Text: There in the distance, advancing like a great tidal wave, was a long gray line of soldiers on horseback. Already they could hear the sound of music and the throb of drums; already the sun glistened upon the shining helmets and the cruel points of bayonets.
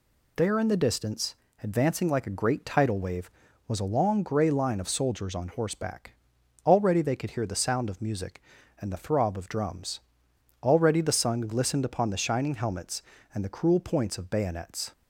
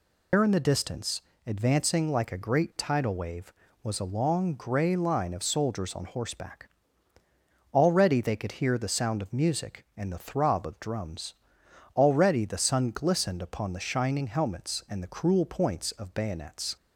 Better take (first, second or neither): first